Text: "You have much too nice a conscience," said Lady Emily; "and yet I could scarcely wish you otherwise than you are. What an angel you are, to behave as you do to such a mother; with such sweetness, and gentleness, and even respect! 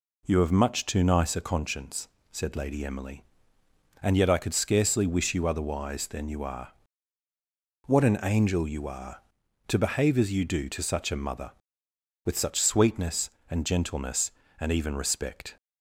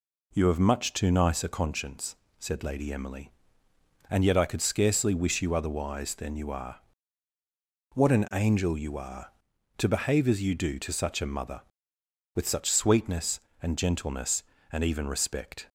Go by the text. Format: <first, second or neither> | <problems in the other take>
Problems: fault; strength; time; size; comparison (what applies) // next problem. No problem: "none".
neither | none